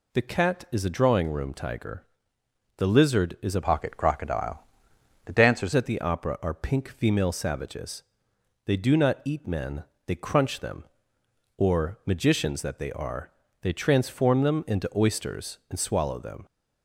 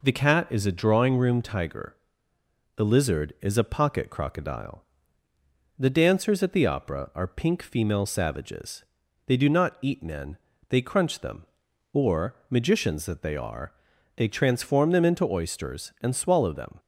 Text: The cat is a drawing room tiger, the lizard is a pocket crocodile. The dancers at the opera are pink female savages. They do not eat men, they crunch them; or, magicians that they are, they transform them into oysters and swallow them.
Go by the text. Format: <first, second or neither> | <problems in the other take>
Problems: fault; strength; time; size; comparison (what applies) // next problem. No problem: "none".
second | changes voice from "pocket" to "dancers"; from 3.6 to 5.7 s; 2.1 s long